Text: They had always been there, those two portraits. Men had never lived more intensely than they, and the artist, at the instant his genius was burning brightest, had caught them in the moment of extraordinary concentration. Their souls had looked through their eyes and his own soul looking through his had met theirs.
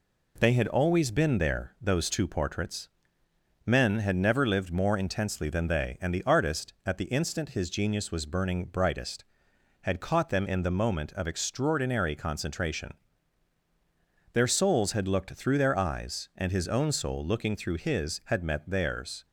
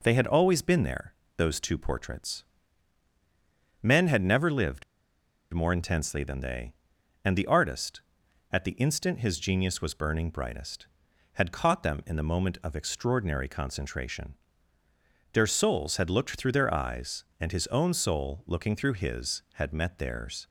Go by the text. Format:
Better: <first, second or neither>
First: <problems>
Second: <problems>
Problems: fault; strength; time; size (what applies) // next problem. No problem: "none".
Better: first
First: none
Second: pauses between "lived" and "more"; noticeable; at 4.8 s; 0.70 s long